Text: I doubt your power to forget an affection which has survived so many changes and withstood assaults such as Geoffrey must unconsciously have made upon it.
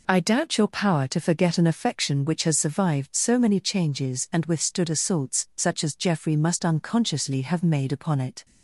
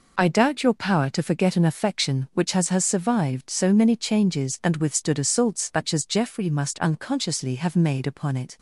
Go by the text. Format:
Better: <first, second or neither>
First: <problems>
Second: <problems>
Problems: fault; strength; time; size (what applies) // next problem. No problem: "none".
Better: first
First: none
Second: says "has" twice; at 2.6 s